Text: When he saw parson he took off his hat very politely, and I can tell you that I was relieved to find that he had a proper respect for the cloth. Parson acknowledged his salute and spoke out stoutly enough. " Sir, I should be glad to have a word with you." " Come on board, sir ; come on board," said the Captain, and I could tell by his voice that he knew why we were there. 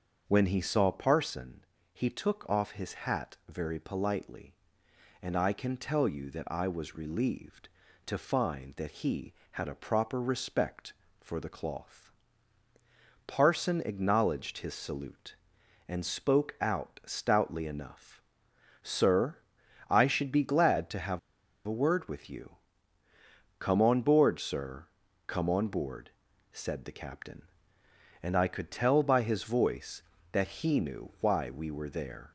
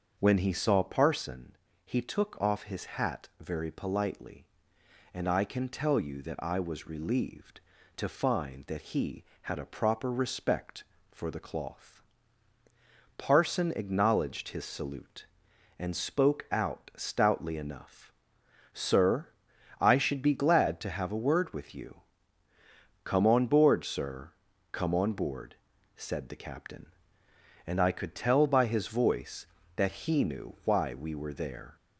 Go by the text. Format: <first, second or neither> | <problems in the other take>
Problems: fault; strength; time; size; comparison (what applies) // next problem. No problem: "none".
second | starts louder than the rest; until 1.2 s; 7 dB; also in the second // pauses between "parson" and "he"; slight; at 1.6 s; 0.30 s long; slight in the second // pauses between "have" and "a"; noticeable; at 21.1 s; 0.47 s long